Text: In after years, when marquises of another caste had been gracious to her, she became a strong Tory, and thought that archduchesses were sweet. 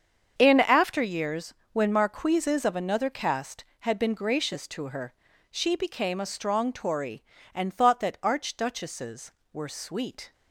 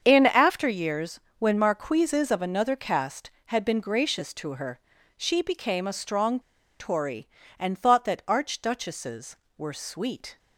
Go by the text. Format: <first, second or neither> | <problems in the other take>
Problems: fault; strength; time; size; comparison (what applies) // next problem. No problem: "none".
first | starts louder than the rest; strong; until 1.0 s; 7 dB; strong in the first // pauses between "strong" and "Tory"; at 6.4 s; 0.39 s long